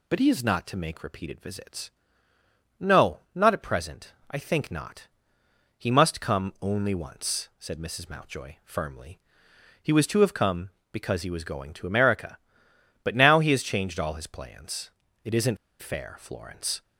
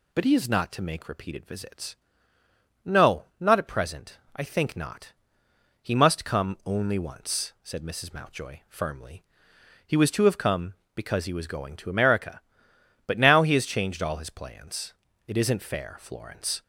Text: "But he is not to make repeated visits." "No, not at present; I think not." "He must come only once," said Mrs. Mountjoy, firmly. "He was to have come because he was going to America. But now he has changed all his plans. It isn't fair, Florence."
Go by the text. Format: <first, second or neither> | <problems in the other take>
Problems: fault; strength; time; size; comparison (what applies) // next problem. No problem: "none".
second | pauses between "isn't" and "fair"; slight; at 15.5 s; 0.24 s long